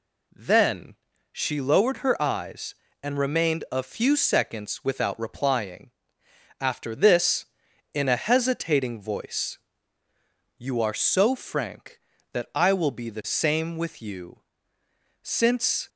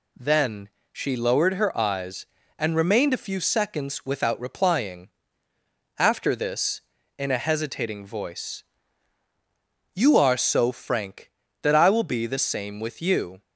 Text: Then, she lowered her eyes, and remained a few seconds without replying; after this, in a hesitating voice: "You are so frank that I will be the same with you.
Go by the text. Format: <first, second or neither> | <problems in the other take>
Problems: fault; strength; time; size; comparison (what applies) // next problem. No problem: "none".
second | goes on to say "Since"; noticeable; from 15.2 s on; 0.68 s long